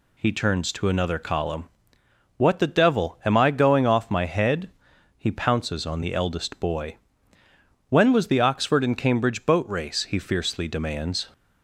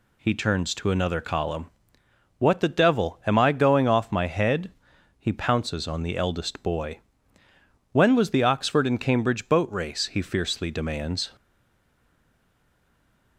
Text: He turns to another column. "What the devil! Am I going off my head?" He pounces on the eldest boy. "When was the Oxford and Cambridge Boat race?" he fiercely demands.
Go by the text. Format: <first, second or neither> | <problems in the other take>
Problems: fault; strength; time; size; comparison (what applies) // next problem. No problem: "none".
first | stays silent after the last word; noticeable; from 11.3 s on; 2.0 s long